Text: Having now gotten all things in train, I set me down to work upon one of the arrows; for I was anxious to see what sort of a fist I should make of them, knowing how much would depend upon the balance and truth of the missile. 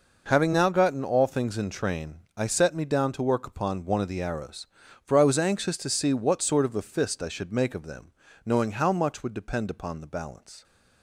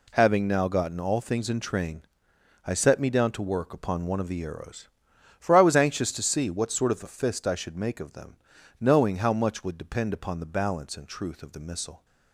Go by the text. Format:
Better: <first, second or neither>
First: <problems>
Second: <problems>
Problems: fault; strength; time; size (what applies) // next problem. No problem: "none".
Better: second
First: stops before "and truth of the missile"; at 10.6 s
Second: none